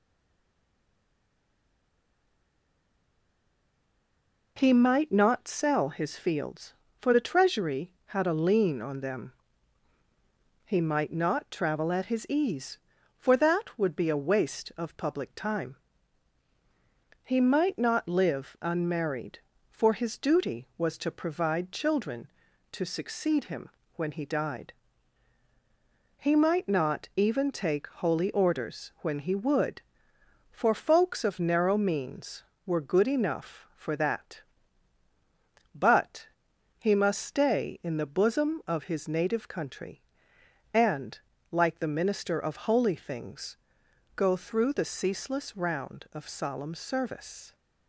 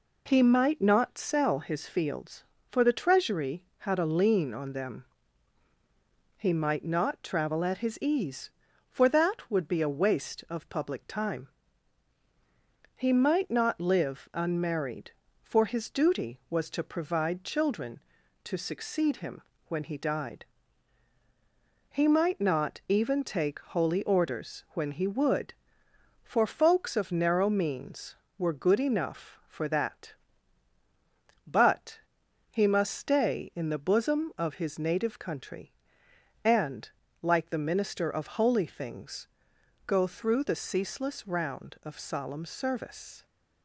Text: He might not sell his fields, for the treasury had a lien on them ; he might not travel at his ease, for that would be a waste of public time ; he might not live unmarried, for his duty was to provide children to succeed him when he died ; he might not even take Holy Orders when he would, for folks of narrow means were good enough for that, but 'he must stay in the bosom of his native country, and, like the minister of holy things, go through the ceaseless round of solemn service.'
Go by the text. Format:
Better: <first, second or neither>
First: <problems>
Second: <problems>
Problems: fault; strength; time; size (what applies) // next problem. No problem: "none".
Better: second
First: stays silent before the first word; strong; until 4.5 s; 4.5 s long // pauses between "him" and "when"; slight; at 23.7 s; 0.24 s long // pauses between "but" and "he"; noticeable; at 36.2 s; 0.50 s long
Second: pauses between "him" and "when"; slight; at 19.4 s; 0.24 s long // pauses between "but" and "he"; noticeable; at 32.0 s; 0.50 s long